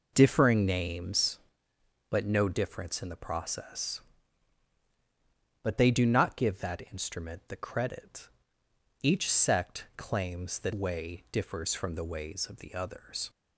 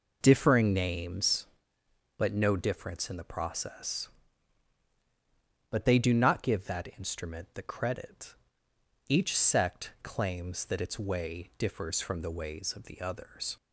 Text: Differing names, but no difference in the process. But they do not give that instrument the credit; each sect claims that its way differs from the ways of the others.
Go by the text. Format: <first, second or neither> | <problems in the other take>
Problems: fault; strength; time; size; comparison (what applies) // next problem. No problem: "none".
second | skips "its"; at 10.7 s